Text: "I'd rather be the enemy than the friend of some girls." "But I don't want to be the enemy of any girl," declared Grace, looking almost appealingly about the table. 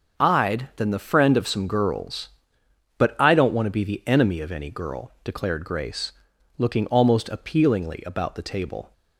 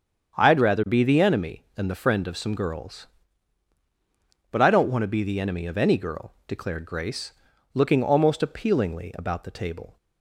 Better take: second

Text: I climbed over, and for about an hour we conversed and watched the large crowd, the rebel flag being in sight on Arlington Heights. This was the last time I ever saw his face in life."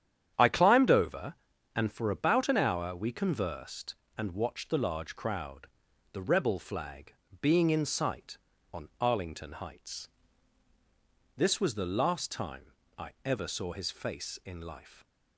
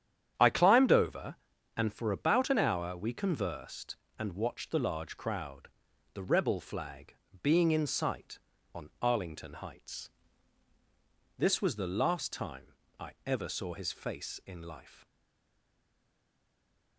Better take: first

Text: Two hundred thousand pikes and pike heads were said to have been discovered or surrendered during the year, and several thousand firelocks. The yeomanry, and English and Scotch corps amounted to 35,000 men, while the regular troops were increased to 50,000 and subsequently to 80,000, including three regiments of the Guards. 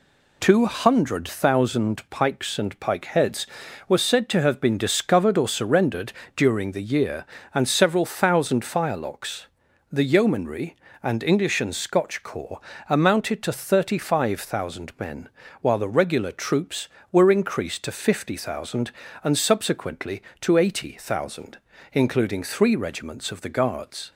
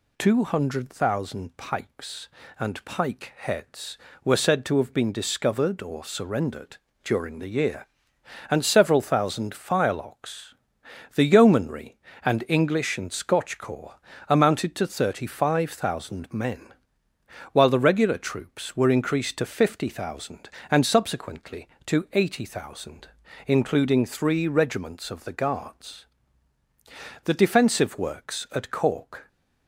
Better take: first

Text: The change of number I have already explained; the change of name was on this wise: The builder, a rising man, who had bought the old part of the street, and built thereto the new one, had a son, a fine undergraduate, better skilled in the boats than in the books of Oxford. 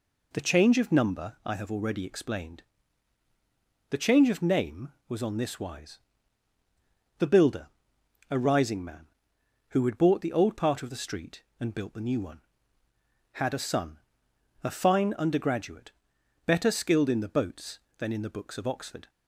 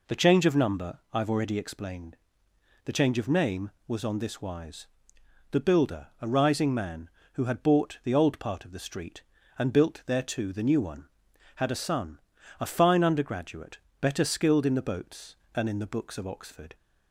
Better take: second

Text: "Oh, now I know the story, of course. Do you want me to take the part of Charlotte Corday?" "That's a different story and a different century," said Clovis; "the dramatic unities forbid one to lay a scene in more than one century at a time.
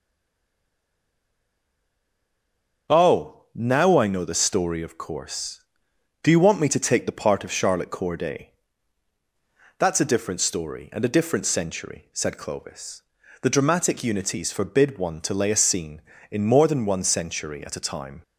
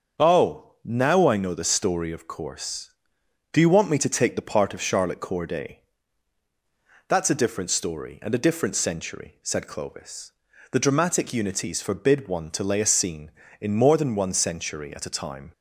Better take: second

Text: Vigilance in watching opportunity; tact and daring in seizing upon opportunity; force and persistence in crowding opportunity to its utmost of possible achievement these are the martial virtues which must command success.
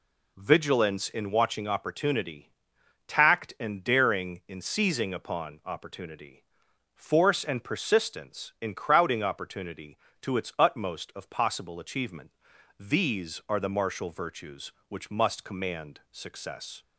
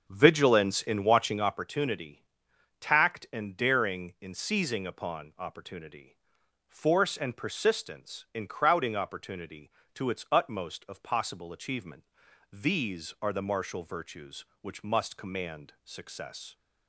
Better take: first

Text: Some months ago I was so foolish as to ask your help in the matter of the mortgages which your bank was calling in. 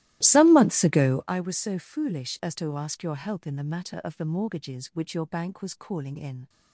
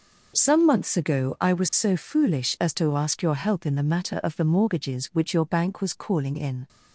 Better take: second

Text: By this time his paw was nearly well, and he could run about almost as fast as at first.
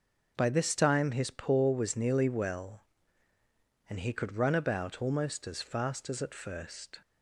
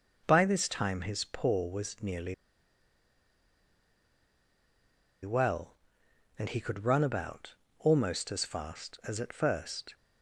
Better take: first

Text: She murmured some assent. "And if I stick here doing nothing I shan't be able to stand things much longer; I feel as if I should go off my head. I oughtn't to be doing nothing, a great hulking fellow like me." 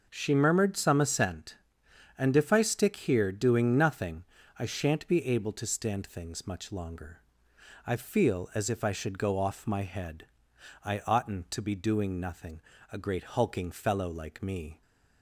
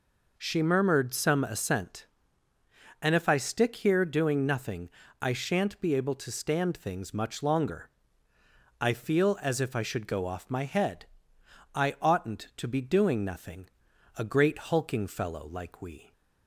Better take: first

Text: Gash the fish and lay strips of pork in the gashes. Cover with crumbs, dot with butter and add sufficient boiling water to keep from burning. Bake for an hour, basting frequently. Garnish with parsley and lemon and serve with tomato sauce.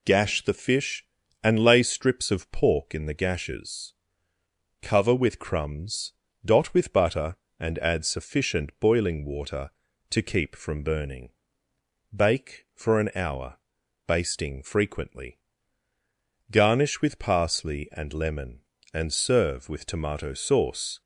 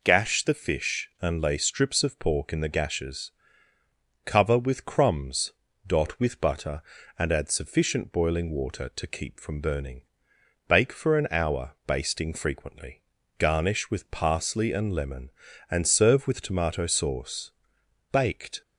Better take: first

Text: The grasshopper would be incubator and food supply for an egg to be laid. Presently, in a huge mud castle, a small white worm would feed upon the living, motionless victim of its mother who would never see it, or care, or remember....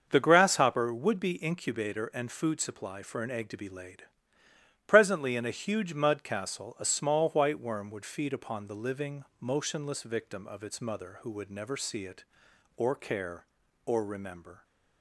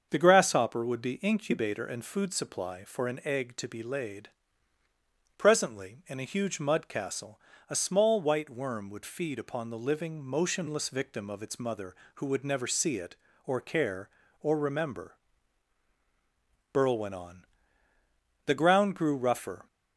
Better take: first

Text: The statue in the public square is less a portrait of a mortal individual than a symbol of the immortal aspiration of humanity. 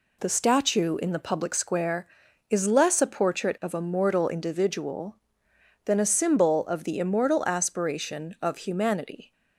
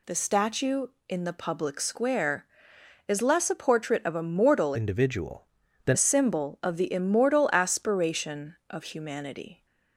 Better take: first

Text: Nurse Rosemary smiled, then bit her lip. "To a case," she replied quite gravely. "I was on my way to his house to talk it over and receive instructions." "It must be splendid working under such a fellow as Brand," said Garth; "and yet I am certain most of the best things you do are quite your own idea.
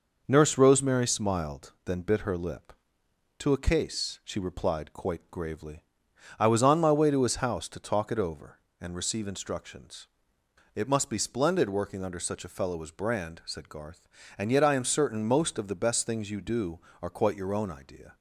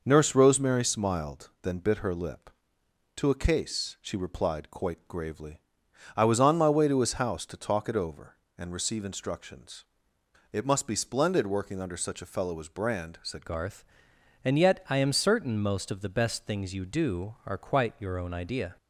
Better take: first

